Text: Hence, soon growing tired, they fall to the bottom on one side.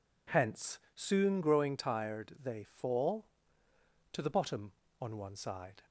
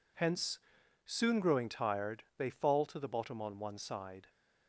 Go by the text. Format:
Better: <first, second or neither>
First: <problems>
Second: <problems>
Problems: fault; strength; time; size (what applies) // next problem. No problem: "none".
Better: neither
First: none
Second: none